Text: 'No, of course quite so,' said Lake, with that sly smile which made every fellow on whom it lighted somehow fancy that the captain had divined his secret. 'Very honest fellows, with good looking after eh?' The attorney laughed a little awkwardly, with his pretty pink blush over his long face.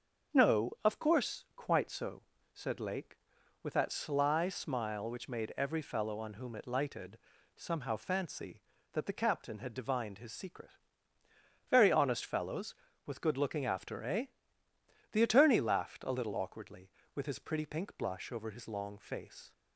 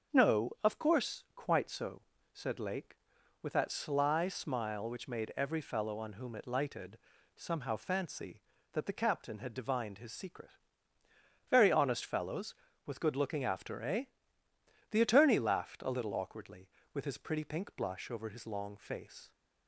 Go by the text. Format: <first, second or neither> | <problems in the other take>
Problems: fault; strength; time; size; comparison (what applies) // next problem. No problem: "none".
neither | starts louder than the rest; the same in both // pauses between "lighted" and "somehow"; the same in both